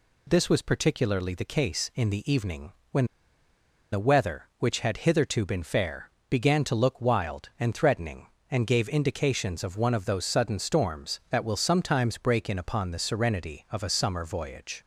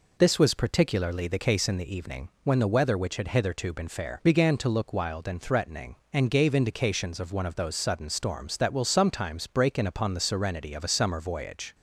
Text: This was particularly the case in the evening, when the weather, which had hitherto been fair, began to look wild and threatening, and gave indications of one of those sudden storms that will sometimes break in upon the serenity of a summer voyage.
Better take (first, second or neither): second